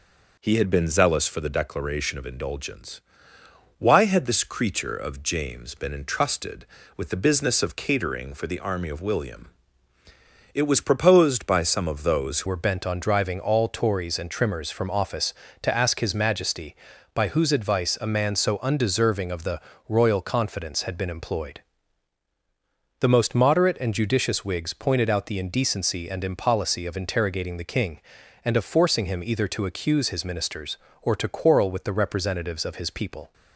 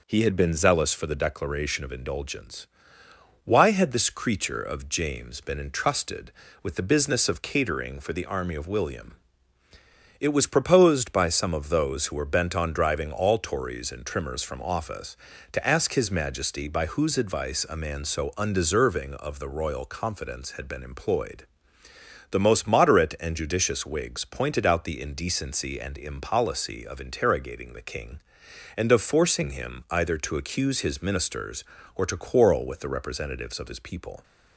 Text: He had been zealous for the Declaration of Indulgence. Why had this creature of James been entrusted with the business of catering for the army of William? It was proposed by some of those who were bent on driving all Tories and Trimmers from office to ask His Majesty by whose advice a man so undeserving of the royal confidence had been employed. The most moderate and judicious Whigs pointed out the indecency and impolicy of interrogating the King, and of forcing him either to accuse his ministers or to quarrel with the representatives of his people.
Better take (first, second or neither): second